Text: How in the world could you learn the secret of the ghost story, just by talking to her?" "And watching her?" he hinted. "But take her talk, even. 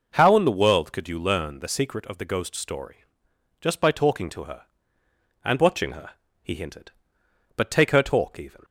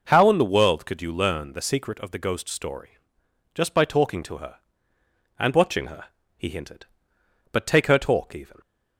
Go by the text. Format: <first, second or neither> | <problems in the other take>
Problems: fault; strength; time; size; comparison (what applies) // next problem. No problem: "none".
neither | none